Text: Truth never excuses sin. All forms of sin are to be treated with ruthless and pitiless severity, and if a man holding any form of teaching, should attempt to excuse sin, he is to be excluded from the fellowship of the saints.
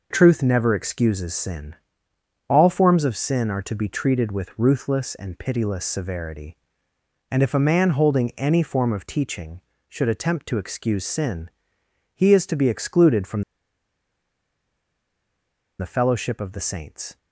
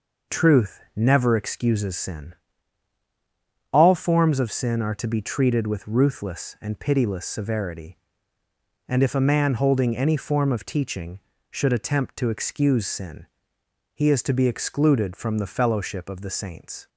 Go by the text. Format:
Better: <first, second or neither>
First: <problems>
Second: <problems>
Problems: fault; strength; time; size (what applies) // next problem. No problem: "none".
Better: second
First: pauses between "from" and "the"; strong; at 13.4 s; 2.3 s long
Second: none